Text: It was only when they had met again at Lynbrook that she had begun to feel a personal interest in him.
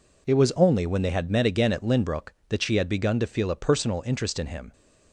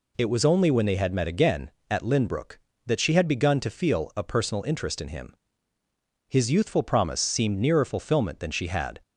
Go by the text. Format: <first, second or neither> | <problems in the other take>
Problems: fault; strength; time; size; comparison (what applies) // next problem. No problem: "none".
first | goes on to say "His youthful promise seemed nearer fulfillment than she had"; strong; from 6.2 s on; 2.7 s long